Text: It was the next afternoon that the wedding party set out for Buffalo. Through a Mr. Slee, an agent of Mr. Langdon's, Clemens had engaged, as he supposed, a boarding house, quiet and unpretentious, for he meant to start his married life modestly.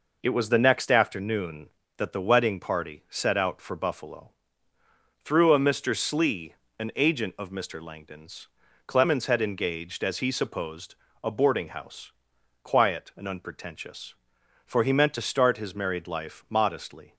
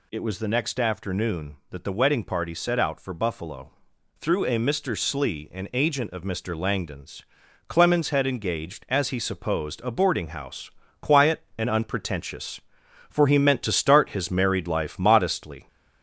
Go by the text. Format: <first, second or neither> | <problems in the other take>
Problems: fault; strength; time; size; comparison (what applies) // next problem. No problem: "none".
first | gets louder; slight; throughout; 3 dB